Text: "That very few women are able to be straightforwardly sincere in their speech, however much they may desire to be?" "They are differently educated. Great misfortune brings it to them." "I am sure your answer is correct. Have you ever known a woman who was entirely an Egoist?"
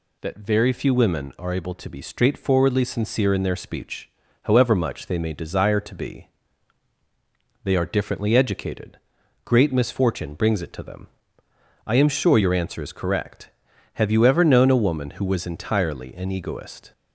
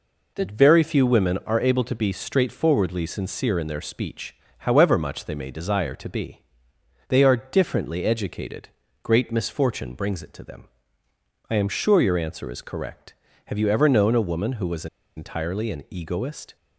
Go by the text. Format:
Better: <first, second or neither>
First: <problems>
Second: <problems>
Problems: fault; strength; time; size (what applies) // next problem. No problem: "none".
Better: first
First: none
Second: pauses between "was" and "entirely"; slight; at 14.8 s; 0.30 s long